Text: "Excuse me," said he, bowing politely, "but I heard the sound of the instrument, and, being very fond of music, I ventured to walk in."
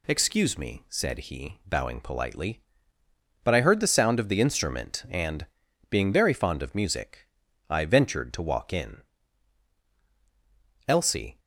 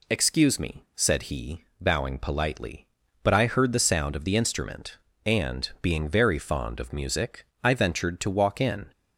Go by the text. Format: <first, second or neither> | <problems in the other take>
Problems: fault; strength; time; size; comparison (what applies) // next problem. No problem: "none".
second | goes on to say "Elsie"; from 10.8 s on; 0.52 s long